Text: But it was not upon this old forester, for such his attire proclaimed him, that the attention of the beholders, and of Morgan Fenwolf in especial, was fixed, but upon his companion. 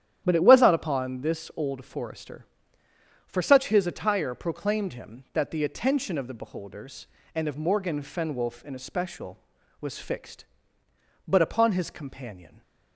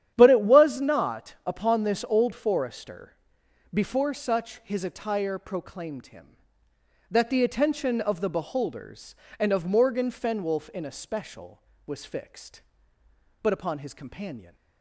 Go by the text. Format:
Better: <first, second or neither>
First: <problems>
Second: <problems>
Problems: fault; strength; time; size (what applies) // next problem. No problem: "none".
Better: first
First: starts louder than the rest; strong; until 1.2 s; 11 dB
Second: starts louder than the rest; strong; until 1.1 s; 10 dB // says "before" for "for"; at 3.7 s